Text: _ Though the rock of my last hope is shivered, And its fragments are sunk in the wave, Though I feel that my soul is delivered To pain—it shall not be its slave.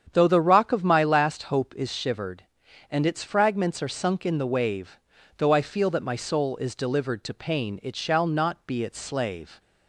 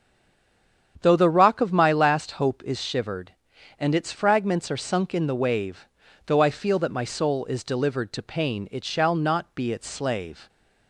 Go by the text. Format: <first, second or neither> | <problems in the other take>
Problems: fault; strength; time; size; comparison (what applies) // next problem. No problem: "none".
first | stays silent before the first word; slight; until 0.9 s; 0.9 s long // starts louder than the rest; strong; until 2.0 s; 8.5 dB; strong in the first